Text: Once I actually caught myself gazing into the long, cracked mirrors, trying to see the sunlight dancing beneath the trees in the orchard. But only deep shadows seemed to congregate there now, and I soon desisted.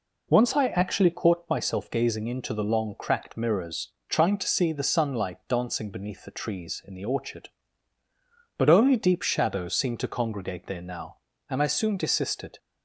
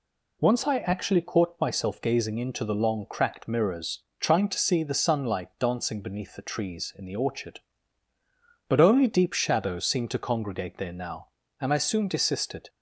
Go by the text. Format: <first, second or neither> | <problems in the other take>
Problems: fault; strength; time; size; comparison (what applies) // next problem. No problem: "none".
second | starts louder than the rest; noticeable; until 1.3 s; 4 dB